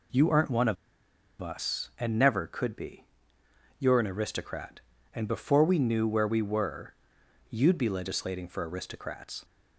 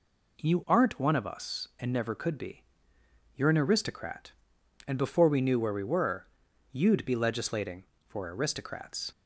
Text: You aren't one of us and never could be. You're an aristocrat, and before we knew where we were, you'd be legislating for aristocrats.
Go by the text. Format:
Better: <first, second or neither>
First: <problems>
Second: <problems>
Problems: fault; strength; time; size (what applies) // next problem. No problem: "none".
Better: second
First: pauses between "of" and "us"; noticeable; at 0.7 s; 0.64 s long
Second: none